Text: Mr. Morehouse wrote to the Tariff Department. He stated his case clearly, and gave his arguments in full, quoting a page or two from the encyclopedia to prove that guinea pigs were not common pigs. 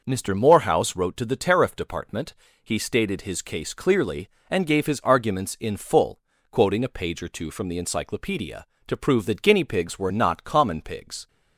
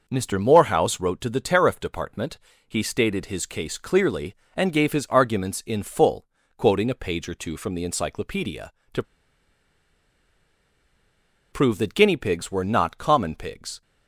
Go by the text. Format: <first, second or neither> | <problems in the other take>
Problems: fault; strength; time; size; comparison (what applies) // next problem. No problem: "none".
first | pauses between "to" and "prove"; strong; at 9.0 s; 2.4 s long